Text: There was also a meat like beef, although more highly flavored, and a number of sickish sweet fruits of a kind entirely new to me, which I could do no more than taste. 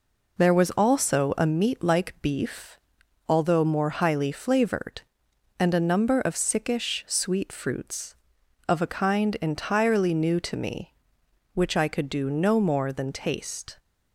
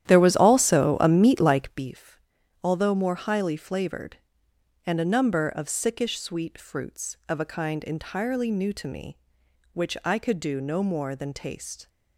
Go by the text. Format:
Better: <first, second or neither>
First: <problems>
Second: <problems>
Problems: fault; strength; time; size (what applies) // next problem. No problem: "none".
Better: first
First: none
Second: starts louder than the rest; strong; until 1.9 s; 11.5 dB